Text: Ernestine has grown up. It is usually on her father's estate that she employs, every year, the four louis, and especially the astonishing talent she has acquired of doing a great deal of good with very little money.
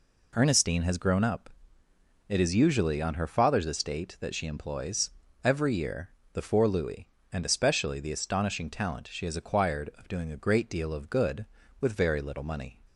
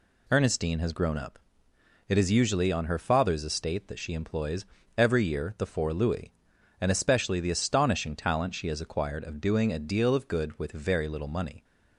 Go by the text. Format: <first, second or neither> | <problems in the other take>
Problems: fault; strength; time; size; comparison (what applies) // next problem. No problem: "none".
first | skips "great"; at 9.7 s